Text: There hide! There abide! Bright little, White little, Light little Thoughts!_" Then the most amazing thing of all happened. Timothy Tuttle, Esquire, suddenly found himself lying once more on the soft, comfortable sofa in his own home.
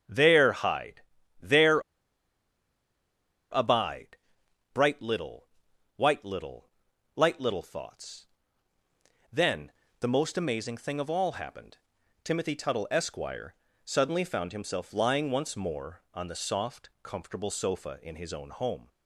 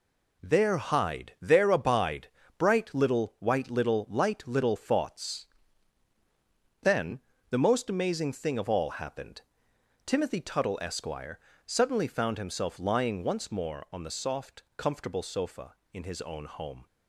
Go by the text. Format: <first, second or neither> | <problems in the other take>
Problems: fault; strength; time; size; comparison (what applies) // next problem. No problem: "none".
second | starts louder than the rest; strong; until 1.4 s; 7.5 dB // pauses between "There" and "abide"; strong; at 1.7 s; 1.7 s long // pauses between "Then" and "the"; slight; at 9.7 s; 0.26 s long; slight in the second